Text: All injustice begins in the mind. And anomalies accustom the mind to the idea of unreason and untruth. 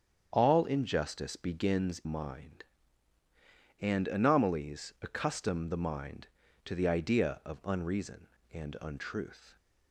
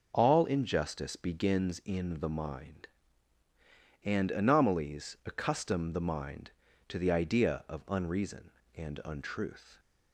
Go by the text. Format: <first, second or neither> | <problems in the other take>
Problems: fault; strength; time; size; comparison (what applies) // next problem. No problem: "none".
second | starts louder than the rest; strong; until 1.3 s; 8 dB // skips "in the"; at 2.0 s